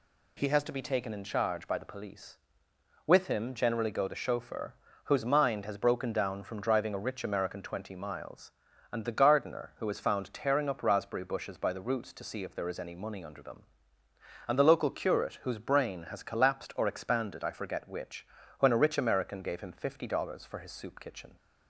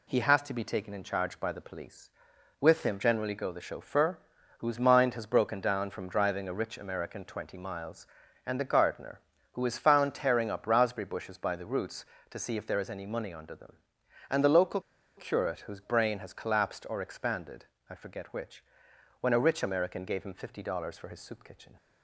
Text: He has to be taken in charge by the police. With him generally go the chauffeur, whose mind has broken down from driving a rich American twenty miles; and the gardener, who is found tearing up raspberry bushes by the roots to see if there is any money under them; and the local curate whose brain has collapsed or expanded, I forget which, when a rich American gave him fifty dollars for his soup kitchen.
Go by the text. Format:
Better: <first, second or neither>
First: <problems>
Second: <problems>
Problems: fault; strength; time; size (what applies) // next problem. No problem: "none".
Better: first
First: none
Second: pauses between "local" and "curate"; at 14.8 s; 0.36 s long